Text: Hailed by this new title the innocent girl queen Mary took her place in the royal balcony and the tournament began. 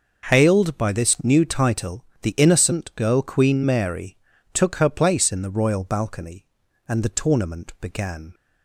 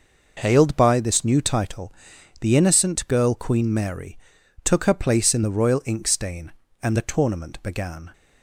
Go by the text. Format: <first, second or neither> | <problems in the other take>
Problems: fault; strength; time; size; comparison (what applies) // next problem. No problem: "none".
first | pauses between "title" and "the"; noticeable; at 1.9 s; 0.50 s long; slight in the first // pauses between "Mary" and "took"; noticeable; at 4.1 s; 0.46 s long; also in the first // says "inkstain" for "balcony"; at 5.8 s